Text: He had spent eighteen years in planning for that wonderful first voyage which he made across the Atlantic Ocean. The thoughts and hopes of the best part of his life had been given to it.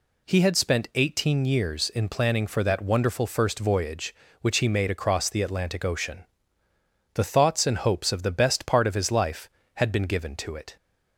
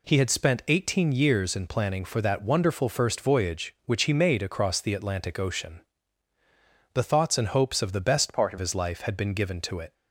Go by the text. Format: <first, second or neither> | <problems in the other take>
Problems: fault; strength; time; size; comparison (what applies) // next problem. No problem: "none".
first | changes voice from "part" to "of"; from 8.3 to 8.5 s; 0.2 s long